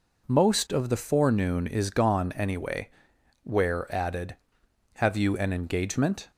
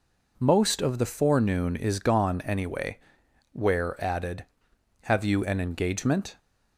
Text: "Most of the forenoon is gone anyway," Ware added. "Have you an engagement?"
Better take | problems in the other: neither | none

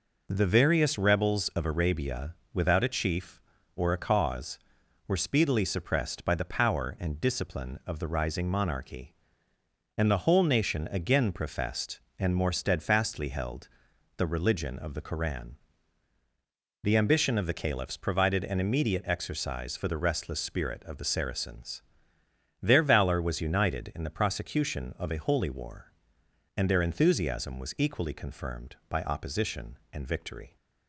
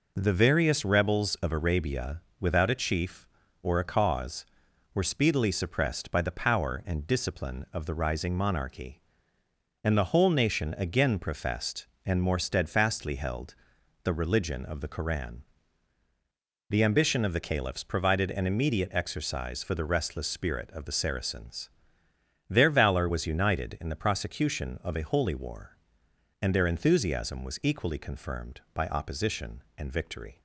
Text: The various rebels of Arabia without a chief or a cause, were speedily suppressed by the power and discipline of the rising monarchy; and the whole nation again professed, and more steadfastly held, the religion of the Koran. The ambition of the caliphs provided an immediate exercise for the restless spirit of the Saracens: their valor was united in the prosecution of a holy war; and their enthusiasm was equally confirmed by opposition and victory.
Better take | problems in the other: neither | pauses between "Arabia" and "without"; slight; the same in both

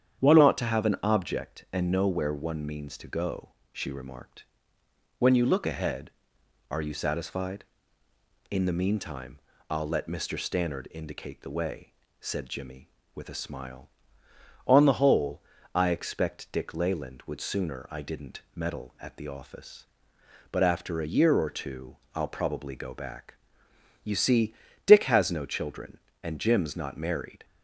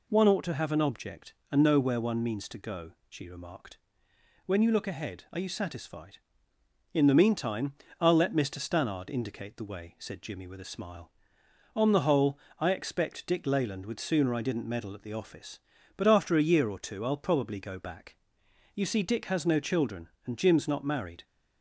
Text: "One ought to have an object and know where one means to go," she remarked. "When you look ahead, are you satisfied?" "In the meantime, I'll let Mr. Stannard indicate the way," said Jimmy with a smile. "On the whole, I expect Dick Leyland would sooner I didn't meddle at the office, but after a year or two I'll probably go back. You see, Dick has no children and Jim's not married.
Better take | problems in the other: second | starts louder than the rest; strong; until 1.2 s; 8.5 dB // changes voice at "ought"; from 0.4 s on; 27.0 s long // pauses between "two" and "I'll"; slight; at 21.9 s; 0.18 s long

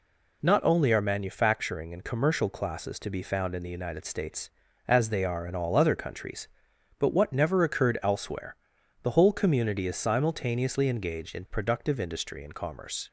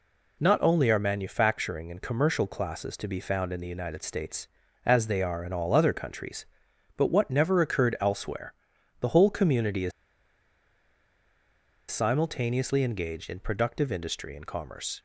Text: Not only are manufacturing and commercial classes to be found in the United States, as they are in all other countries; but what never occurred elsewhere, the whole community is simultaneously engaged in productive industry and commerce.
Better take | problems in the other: first | pauses between "is" and "simultaneously"; strong; at 9.9 s; 1.9 s long

